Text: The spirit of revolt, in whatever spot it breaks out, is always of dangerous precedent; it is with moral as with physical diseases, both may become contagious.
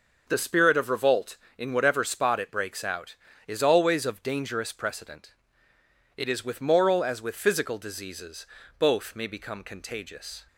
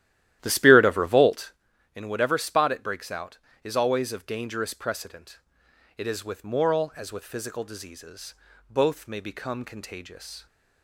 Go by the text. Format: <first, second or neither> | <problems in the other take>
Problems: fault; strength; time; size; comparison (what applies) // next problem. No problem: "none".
first | starts louder than the rest; strong; until 1.6 s; 13 dB